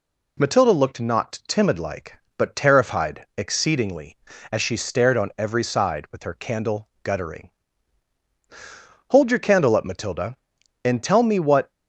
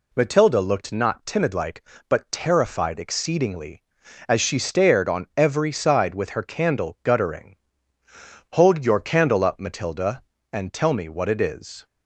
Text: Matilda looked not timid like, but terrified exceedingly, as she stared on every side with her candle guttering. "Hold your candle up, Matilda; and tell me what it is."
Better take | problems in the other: second | pauses between "candle" and "guttering"; slight; at 6.8 s; 0.16 s long // stops before "it is"; at 11.7 s

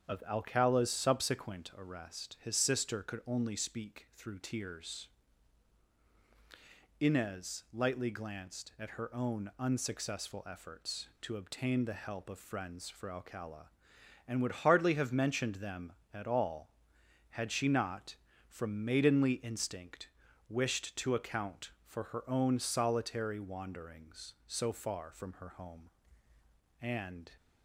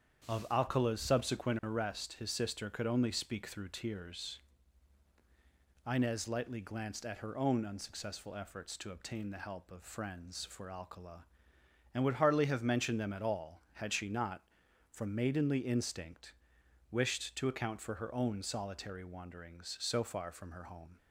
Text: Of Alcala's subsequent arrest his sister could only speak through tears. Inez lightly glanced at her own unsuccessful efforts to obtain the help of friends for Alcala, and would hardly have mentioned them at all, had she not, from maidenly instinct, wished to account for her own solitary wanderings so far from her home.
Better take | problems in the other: second | starts louder than the rest; strong; until 1.0 s; 7.5 dB; strong in the second // goes on to say "And"; from 26.8 s on; 0.50 s long

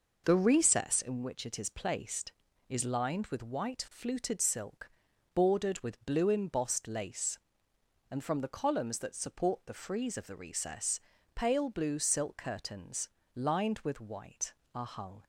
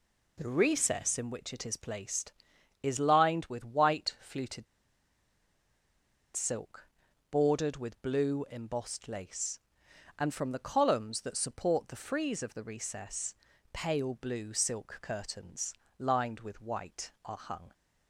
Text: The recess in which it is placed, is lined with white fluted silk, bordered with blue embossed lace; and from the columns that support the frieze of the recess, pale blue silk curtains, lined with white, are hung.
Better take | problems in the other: first | pauses between "fluted" and "silk"; strong; at 4.6 s; 1.7 s long

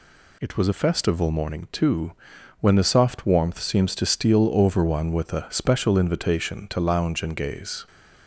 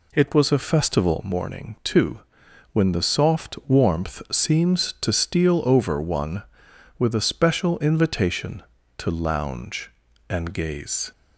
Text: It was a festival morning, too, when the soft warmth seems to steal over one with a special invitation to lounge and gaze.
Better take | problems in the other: neither | none

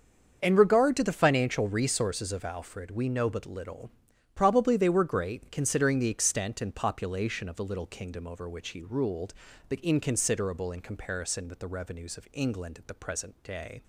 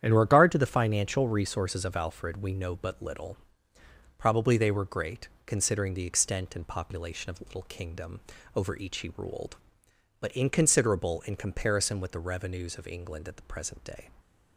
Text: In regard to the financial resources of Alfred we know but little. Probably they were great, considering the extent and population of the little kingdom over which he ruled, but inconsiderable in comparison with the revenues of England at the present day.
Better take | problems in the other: first | starts louder than the rest; strong; until 1.0 s; 9.5 dB; also in the first // pauses between "kingdom" and "over"; slight; at 8.1 s; 0.36 s long // says "each" for "which"; at 8.7 s

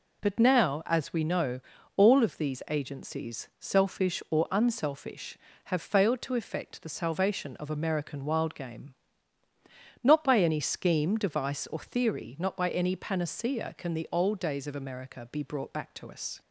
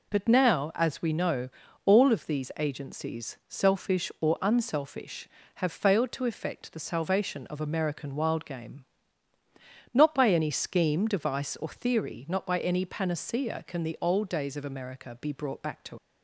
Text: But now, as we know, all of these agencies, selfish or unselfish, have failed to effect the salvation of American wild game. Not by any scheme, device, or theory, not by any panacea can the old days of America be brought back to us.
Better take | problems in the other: first | stops before "us"; at 15.9 s

